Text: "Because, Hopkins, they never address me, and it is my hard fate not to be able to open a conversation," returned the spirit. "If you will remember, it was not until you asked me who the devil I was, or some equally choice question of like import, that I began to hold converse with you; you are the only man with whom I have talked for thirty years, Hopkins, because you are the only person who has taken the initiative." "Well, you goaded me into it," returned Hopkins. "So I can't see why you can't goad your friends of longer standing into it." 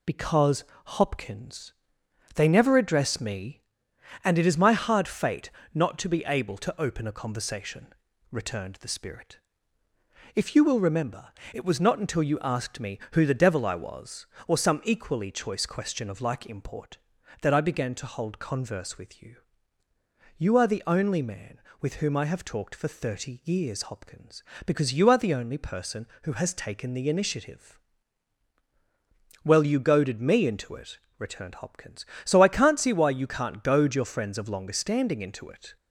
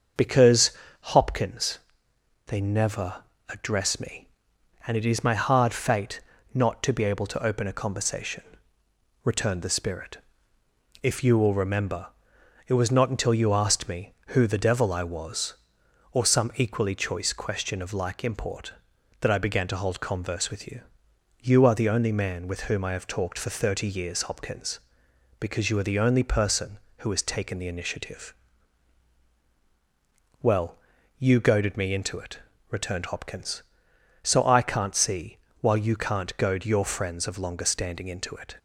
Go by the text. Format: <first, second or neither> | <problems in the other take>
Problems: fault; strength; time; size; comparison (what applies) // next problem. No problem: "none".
first | starts louder than the rest; until 1.4 s; 6.5 dB // pauses between "never" and "address"; slight; at 3.2 s; 0.26 s long // pauses between "fate" and "not"; slight; at 6.1 s; 0.34 s long; slight in the first // says "while" for "why"; at 35.6 s